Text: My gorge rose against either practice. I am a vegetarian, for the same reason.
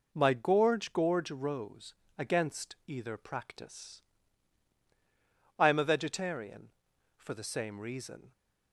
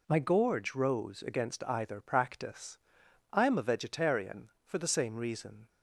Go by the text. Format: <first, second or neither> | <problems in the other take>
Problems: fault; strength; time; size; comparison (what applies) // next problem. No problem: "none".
second | says "gorge" twice; at 0.9 s // pauses between "rose" and "against"; slight; at 1.9 s; 0.24 s long